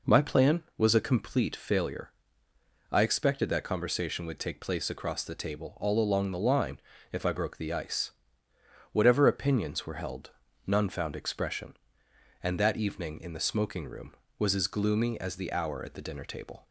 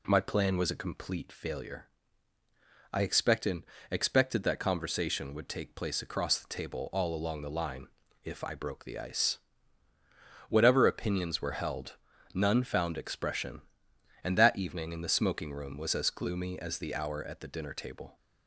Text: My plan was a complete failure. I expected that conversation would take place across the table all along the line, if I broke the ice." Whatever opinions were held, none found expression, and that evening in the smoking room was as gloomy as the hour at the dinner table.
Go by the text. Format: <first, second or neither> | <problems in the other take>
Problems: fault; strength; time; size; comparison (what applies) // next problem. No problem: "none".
first | says "expected" twice; at 3.8 s